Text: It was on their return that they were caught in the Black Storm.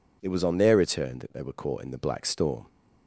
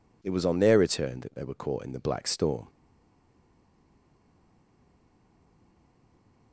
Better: first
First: none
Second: stays silent after the last word; strong; from 2.6 s on; 3.9 s long

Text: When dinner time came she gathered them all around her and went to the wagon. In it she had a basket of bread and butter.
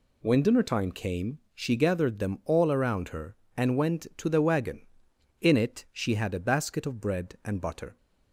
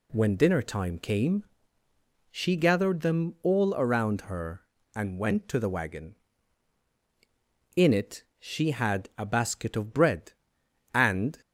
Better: first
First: none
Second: pauses between "came" and "she"; noticeable; at 1.4 s; 0.88 s long // stops before "butter"; at 11.4 s

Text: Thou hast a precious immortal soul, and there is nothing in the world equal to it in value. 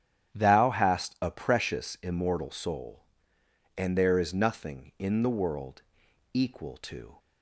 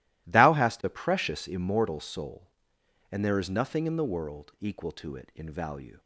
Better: second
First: starts louder than the rest; strong; until 1.3 s; 10 dB // pauses between "world" and "equal"; noticeable; at 5.8 s; 0.54 s long // stops before "it in value"; at 7.1 s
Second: none

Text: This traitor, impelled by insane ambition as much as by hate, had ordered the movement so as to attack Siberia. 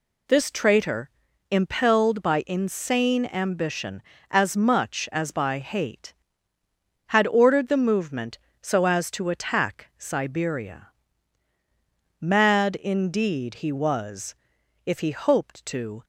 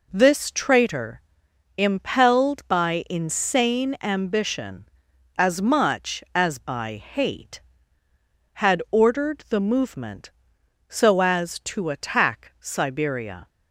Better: second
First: goes on to say "Mad indeed he was if he hoped to"; strong; from 12.2 s on; 3.8 s long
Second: none

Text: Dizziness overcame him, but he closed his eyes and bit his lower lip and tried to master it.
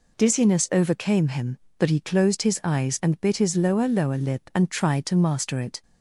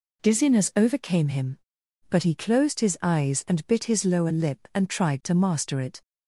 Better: second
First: says "lower" twice; at 3.8 s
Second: none

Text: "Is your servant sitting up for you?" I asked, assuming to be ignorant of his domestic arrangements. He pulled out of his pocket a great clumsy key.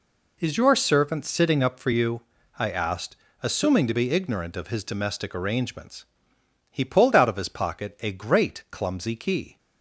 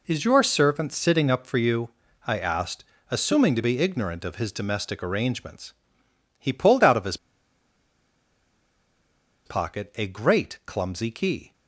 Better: first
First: none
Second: pauses between "his" and "pocket"; strong; at 7.1 s; 2.2 s long

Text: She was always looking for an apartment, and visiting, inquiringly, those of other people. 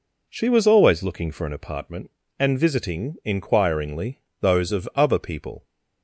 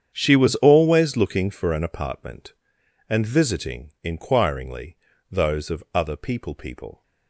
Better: first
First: none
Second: starts louder than the rest; strong; until 1.1 s; 8.5 dB // says "people" twice; at 6.5 s

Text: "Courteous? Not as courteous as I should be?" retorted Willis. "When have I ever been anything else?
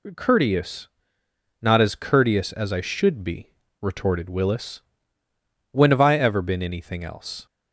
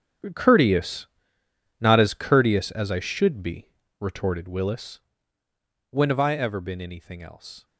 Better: first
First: none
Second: gets quieter; strong; throughout; 16.5 dB

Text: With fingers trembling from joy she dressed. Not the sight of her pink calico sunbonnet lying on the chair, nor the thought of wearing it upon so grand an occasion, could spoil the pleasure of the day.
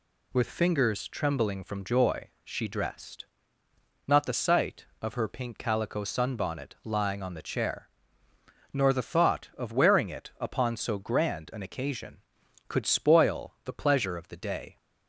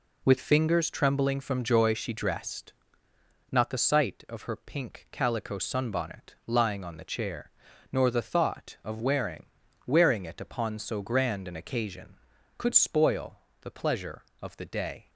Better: first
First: none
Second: says "wearing" twice; at 9.8 s // pauses between "spoil" and "the"; slight; at 13.3 s; 0.24 s long

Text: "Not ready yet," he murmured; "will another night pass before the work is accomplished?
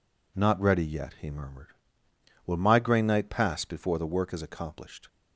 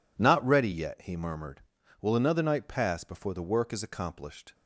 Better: second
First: says "migraine" for "another"; at 2.5 s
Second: none

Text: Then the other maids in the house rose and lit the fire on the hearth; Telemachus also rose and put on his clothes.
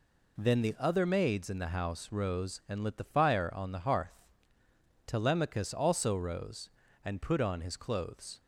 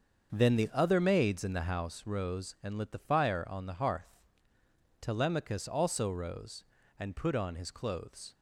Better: first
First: none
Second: starts louder than the rest; until 1.8 s; 7 dB

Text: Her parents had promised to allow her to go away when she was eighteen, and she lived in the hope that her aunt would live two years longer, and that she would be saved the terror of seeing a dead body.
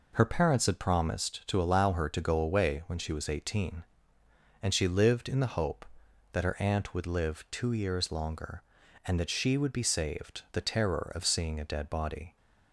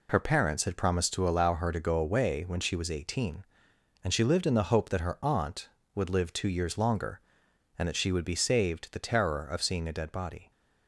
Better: neither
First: none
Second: none

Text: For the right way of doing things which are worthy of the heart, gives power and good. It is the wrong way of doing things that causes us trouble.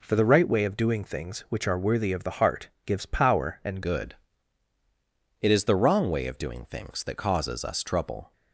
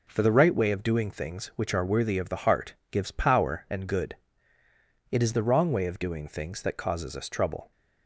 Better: second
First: changes voice at "good"; from 3.8 s on; 4.5 s long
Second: none

